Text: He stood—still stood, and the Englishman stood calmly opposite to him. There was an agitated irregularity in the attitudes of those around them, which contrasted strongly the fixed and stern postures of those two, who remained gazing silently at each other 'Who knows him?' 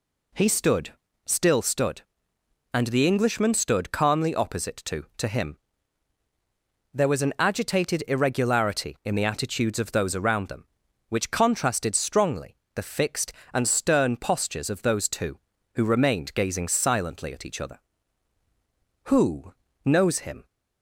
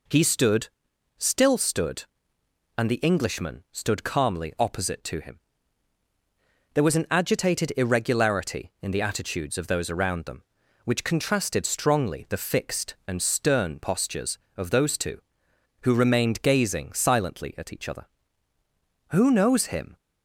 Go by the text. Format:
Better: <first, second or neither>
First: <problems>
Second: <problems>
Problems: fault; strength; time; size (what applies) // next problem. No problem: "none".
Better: second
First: says "to" twice; at 5.1 s // pauses between "strongly" and "the"; slight; at 12.5 s; 0.18 s long // pauses between "Who" and "knows"; slight; at 19.5 s; 0.32 s long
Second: none